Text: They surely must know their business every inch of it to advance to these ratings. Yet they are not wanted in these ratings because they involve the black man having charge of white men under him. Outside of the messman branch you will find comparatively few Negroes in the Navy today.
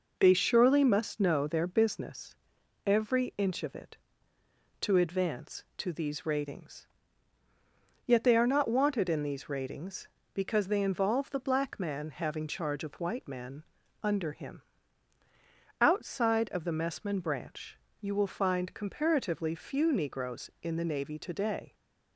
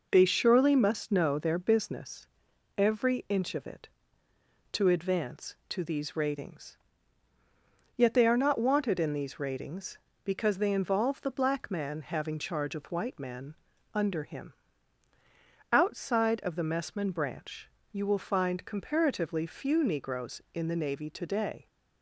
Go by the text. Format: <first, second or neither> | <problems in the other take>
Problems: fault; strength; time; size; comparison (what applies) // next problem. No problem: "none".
neither | pauses between "business" and "every"; noticeable; the same in both // pauses between "men" and "under"; the same in both // pauses between "branch" and "you"; slight; the same in both